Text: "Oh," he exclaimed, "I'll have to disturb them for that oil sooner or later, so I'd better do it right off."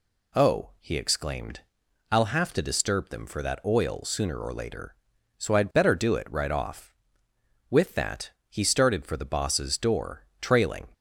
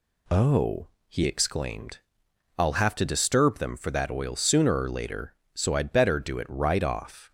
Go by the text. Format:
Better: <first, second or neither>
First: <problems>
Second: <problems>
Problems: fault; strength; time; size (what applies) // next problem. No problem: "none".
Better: second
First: goes on to say "With that he started for the boss's door trailing"; strong; from 7.6 s on; 3.1 s long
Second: none